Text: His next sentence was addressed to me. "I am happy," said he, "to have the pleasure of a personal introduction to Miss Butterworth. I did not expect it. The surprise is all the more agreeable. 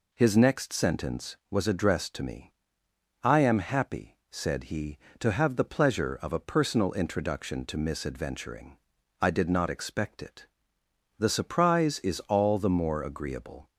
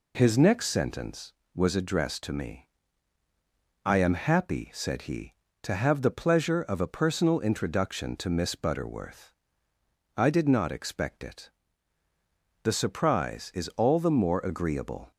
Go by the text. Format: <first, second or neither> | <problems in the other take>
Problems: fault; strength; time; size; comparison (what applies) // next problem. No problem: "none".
second | says "Adventuring" for "Butterworth"; at 8.0 s